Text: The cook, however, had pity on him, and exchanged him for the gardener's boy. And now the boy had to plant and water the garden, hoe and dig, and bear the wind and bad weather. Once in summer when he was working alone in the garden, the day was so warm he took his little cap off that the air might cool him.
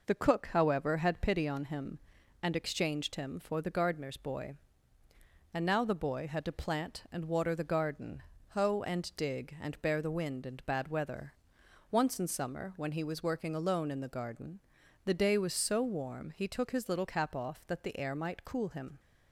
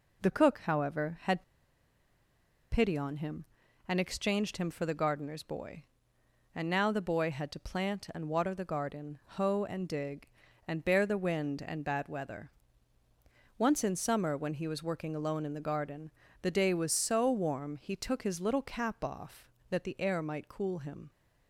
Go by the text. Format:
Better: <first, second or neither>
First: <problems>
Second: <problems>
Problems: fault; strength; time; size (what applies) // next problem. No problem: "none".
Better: first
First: none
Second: pauses between "had" and "pity"; strong; at 1.4 s; 1.2 s long